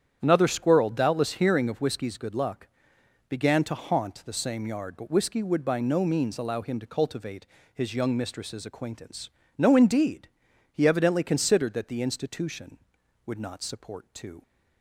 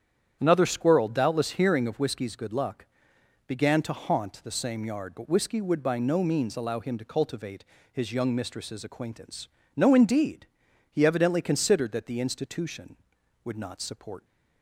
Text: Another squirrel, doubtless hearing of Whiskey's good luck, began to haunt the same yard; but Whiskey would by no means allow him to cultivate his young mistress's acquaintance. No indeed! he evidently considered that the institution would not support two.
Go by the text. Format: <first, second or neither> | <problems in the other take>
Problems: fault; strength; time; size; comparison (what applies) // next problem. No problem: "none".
first | starts louder than the rest; strong; until 1.4 s; 9 dB; strong in the first // pauses between "cultivate" and "his"; slight; at 7.6 s; 0.26 s long; slight in the first // stops before "two"; at 14.2 s